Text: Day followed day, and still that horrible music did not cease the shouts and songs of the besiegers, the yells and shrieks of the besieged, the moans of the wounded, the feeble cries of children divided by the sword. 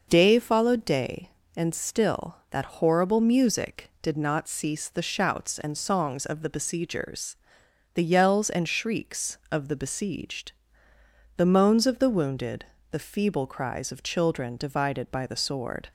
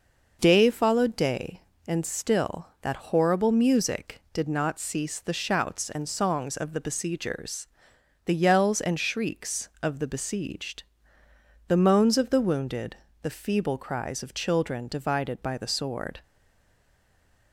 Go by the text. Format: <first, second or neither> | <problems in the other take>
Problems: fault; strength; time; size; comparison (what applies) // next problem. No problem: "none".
first | stays silent after the last word; noticeable; from 16.2 s on; 1.3 s long